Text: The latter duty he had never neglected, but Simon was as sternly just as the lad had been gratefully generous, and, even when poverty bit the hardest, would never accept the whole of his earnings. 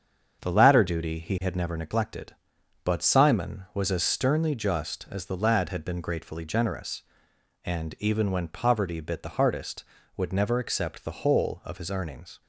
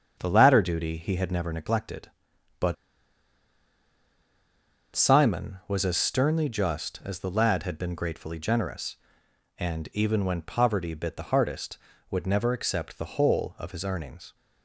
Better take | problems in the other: first | starts louder than the rest; until 1.1 s; 7 dB; also in the first // pauses between "but" and "Simon"; strong; at 2.7 s; 2.1 s long

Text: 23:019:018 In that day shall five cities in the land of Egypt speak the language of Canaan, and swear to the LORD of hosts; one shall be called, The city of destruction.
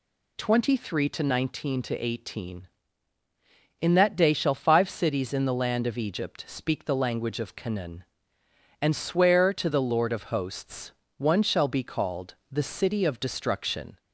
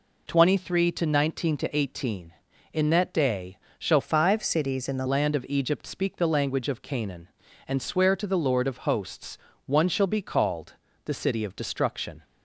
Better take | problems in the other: first | pauses between "day" and "shall"; slight; at 3.5 s; 0.20 s long // changes voice from "five" to "the"; from 4.0 to 5.0 s; 1.0 s long

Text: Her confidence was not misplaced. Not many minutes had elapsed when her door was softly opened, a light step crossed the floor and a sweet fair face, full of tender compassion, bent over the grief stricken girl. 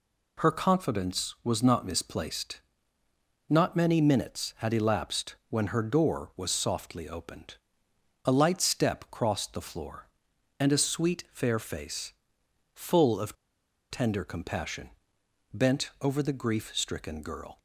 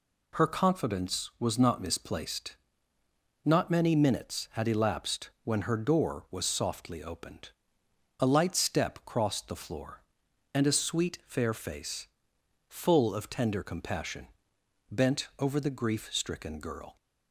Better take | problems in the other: second | pauses between "of" and "tender"; noticeable; at 13.3 s; 0.56 s long

